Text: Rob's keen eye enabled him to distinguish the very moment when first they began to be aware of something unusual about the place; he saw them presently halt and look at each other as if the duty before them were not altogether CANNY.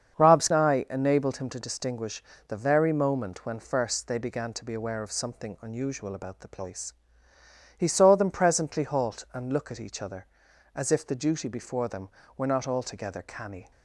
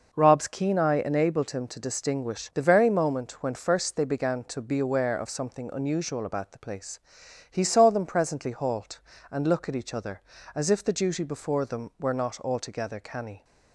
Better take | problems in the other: second | starts louder than the rest; strong; until 1.2 s; 7 dB // skips "keen"; at 0.5 s // pauses between "distinguish" and "the"; slight; at 2.2 s; 0.26 s long

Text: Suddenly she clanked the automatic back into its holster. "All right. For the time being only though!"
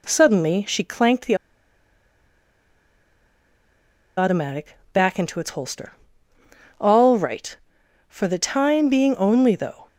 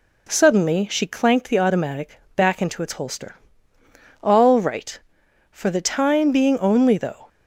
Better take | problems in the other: second | pauses between "the" and "automatic"; strong; at 1.3 s; 2.8 s long // pauses between "automatic" and "back"; slight; at 4.7 s; 0.16 s long; slight in the second

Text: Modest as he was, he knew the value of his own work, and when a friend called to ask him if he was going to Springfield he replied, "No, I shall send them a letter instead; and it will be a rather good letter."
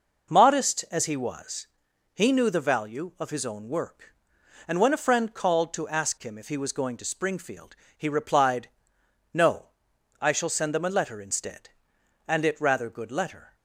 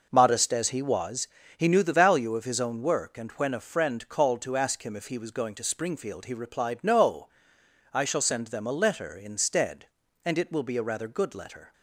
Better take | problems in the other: second | pauses between "Springfield" and "he"; slight; at 7.7 s; 0.22 s long // skips "will be a"; at 12.6 s

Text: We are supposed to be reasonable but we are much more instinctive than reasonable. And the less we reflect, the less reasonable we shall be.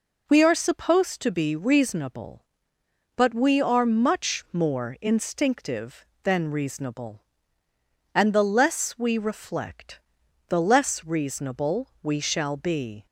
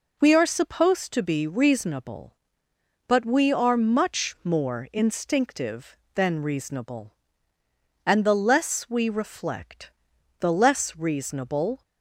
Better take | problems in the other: first | stops before "we shall be"; at 11.8 s

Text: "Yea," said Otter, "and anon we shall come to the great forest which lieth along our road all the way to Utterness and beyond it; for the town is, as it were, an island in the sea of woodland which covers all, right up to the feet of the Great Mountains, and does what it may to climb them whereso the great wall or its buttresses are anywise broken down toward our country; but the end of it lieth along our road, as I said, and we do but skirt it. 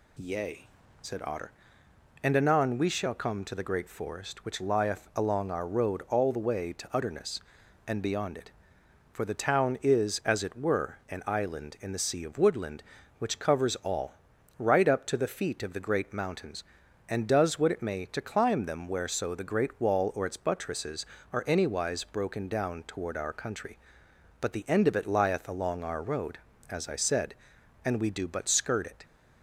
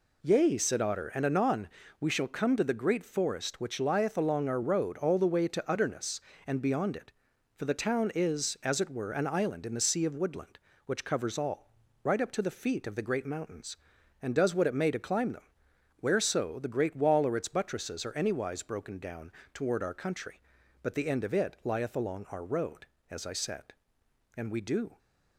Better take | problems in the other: first | pauses between "anon" and "we"; slight; at 1.6 s; 0.32 s long // pauses between "them" and "whereso"; noticeable; at 15.4 s; 0.58 s long // pauses between "down" and "toward"; slight; at 19.2 s; 0.24 s long // stops before "but skirt it"; at 24.9 s

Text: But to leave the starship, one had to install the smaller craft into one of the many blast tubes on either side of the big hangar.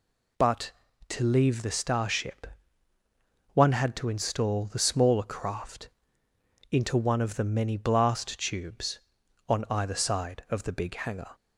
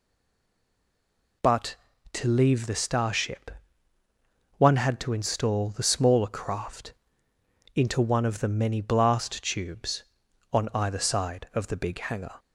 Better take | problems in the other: first | stays silent before the first word; noticeable; until 1.4 s; 1.4 s long // pauses between "craft" and "into"; noticeable; at 6.9 s; 0.82 s long; noticeable in the first

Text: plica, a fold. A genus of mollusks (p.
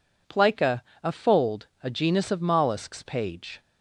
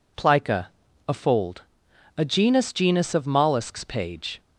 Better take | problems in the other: first | says "genus" twice; at 2.7 s

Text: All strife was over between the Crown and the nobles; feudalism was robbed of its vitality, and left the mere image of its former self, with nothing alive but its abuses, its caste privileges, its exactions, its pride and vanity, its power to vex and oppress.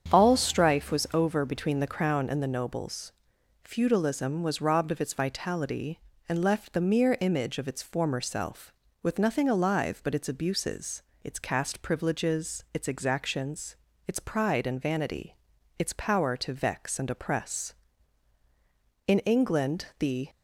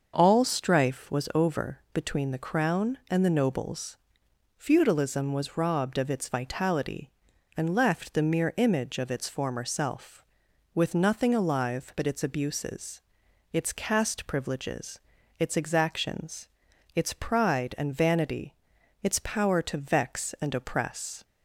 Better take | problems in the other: second | starts louder than the rest; strong; until 1.1 s; 8 dB; also in the second // goes on to say "In England the"; noticeable; from 19.0 s on; 1.2 s long

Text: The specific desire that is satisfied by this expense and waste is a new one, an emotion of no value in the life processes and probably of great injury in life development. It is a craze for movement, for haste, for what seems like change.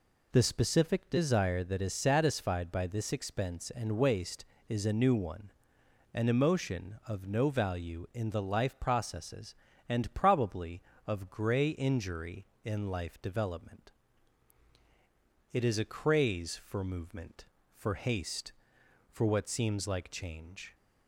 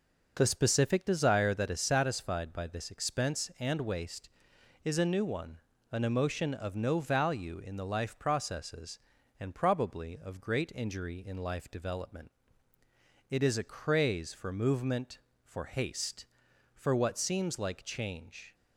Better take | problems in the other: second | says "grey" for "great"; at 11.3 s

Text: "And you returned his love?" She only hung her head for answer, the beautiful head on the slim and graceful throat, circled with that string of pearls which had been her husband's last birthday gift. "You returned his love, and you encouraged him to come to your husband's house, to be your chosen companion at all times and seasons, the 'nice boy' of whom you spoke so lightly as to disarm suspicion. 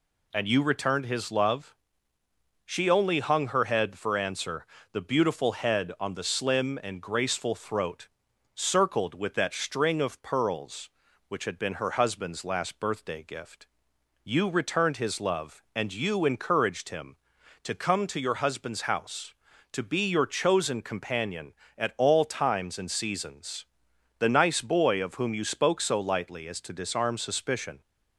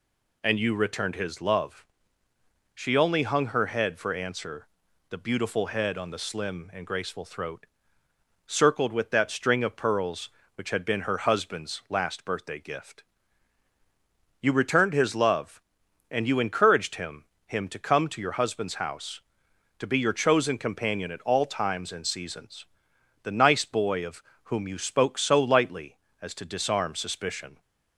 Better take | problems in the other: first | says "him" twice; at 17.4 s // pauses between "of" and "whom"; slight; at 24.2 s; 0.22 s long

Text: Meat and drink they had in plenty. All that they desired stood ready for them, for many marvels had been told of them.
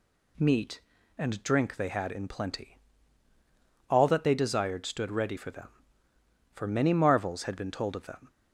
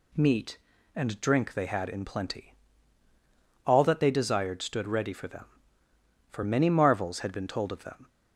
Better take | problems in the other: neither | none

